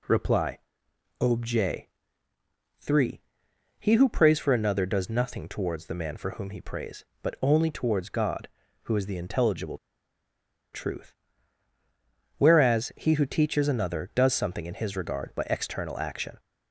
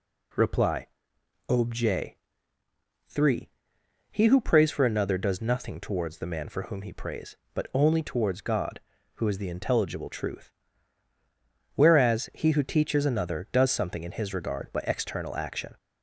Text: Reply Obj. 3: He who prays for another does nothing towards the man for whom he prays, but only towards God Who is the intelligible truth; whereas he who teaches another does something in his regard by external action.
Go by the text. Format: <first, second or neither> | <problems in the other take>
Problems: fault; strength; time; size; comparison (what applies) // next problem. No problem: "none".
second | pauses between "Reply" and "Obj"; noticeable; at 0.5 s; 0.62 s long; noticeable in the second // pauses between "intelligible" and "truth"; noticeable; at 9.7 s; 0.96 s long